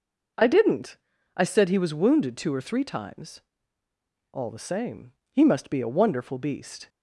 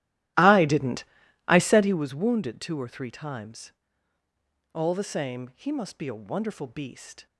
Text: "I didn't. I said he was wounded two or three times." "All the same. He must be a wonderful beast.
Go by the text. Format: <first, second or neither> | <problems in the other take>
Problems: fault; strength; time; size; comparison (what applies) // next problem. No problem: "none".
first | starts louder than the rest; strong; until 2.1 s; 15 dB